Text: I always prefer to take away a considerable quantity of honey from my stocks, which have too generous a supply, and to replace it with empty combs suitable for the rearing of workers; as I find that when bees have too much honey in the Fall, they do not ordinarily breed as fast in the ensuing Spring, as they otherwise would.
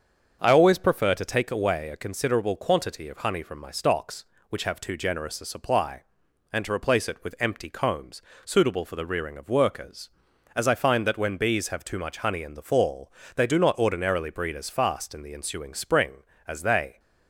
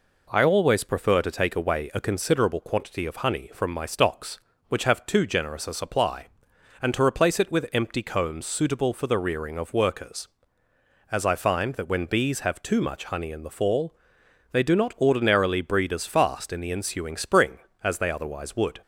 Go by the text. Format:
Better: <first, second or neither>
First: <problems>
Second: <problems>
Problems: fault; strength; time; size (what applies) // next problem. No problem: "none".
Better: second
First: starts louder than the rest; until 1.4 s; 7 dB // pauses between "combs" and "suitable"; slight; at 8.2 s; 0.24 s long // stops before "otherwise would"; at 16.9 s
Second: none